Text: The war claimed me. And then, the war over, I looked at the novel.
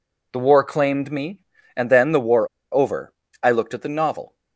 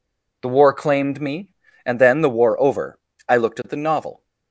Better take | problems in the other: second | pauses between "war" and "over"; slight; at 2.4 s; 0.26 s long

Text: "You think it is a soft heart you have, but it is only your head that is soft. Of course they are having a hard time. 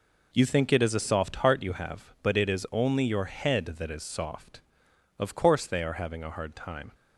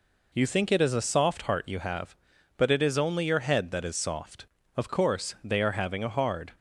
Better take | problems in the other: first | stops before "time"; at 6.5 s

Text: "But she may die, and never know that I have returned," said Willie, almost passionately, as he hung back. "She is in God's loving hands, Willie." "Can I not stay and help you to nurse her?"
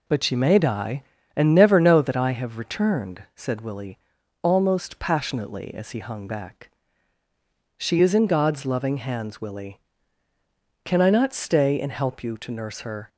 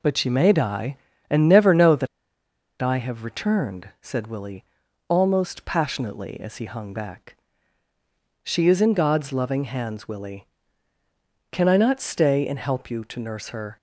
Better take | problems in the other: first | pauses between "that" and "I"; noticeable; at 2.0 s; 0.75 s long

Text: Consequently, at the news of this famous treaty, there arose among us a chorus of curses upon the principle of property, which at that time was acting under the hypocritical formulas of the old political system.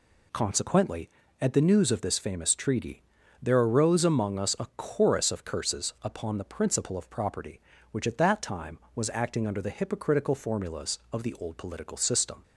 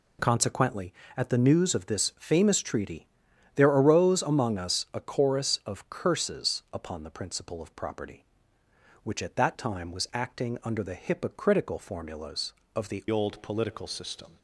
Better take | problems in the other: first | changes voice at "old"; from 13.1 s on; 1.2 s long

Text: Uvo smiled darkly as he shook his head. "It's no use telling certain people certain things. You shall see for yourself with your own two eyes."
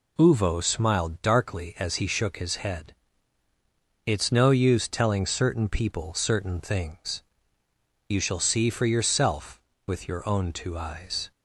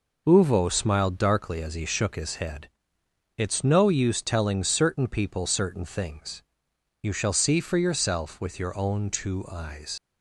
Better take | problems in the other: first | leaves "eyes" unfinished; at 9.9 s; 65 ms

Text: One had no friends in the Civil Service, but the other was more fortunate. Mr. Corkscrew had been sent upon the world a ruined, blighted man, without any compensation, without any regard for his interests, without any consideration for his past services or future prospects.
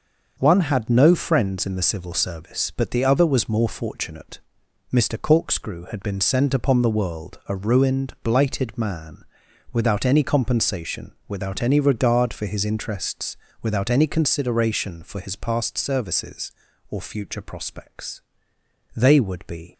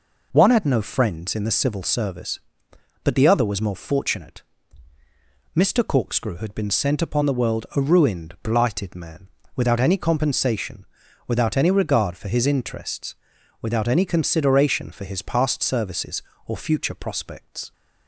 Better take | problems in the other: second | starts louder than the rest; until 1.4 s; 6.5 dB // goes on to say "They would be"; noticeable; from 18.9 s on; 0.78 s long

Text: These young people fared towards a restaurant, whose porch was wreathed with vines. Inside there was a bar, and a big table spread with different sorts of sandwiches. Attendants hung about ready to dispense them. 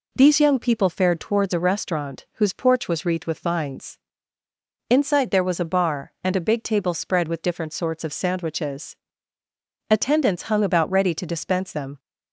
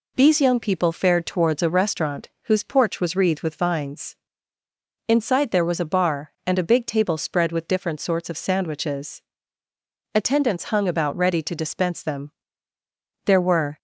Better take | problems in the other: first | goes on to say "There were"; from 13.2 s on; 0.52 s long

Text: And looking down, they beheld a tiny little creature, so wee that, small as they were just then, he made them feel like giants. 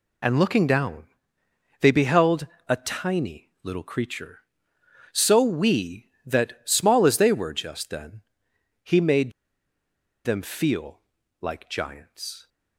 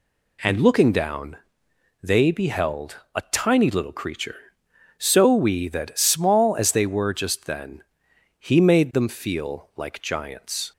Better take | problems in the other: second | pauses between "beheld" and "a"; slight; at 2.4 s; 0.22 s long; slight in the second // pauses between "made" and "them"; noticeable; at 9.3 s; 0.94 s long // pauses between "feel" and "like"; at 10.9 s; 0.42 s long

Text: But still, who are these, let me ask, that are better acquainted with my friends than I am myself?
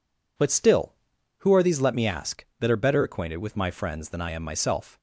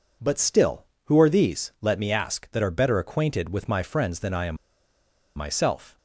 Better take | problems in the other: first | pauses between "am" and "myself"; noticeable; at 4.5 s; 0.80 s long

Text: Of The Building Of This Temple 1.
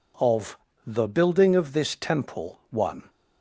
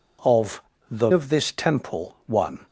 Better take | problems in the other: first | pauses between "Of" and "The"; slight; at 0.6 s; 0.30 s long; slight in the first // skips "Building"; at 1.1 s

